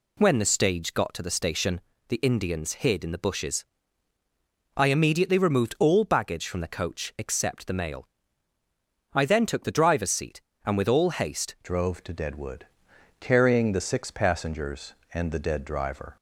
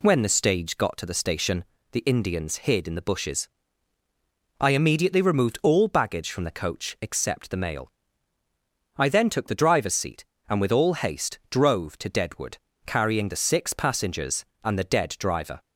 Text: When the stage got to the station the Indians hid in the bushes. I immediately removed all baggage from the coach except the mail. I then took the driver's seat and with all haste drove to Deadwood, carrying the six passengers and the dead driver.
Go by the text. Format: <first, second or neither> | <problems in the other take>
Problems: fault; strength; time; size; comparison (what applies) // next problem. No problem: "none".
second | pauses between "station" and "the"; slight; at 1.8 s; 0.28 s long; slight in the second // changes voice at "drove"; from 11.6 s on; 4.5 s long